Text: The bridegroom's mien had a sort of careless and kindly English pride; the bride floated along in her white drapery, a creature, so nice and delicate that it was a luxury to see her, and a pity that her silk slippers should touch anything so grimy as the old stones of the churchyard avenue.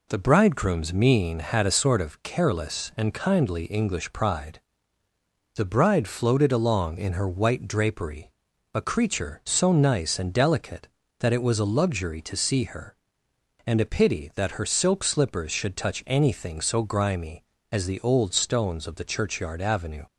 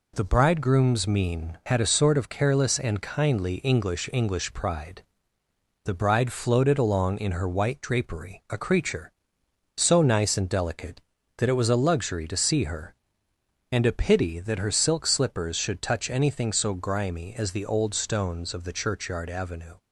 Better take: first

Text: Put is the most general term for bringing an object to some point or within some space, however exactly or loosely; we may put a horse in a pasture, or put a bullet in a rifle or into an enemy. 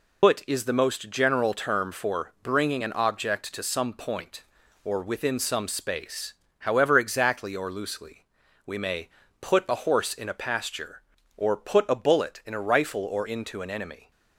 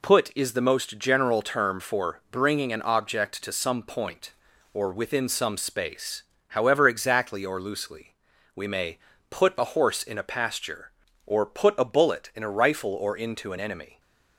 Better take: second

